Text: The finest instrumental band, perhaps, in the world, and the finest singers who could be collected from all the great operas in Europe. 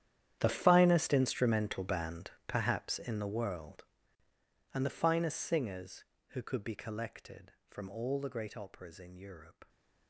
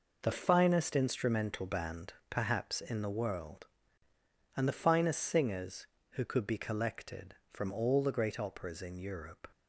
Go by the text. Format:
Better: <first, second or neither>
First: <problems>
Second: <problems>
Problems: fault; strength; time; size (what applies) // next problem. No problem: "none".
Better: second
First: gets quieter; strong; throughout; 17.5 dB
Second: none